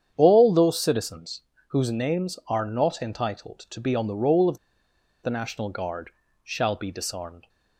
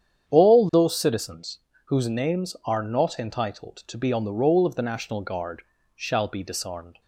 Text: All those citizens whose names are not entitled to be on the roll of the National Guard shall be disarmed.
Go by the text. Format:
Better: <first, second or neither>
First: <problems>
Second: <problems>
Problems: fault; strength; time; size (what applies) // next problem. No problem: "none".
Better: second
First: starts louder than the rest; strong; until 1.1 s; 8.5 dB // pauses between "citizens" and "whose"; slight; at 1.4 s; 0.28 s long // pauses between "of" and "the"; noticeable; at 4.5 s; 0.66 s long // pauses between "Guard" and "shall"; slight; at 6.1 s; 0.34 s long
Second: starts louder than the rest; strong; until 1.3 s; 8.5 dB // pauses between "citizens" and "whose"; slight; at 1.5 s; 0.28 s long // pauses between "Guard" and "shall"; slight; at 5.6 s; 0.34 s long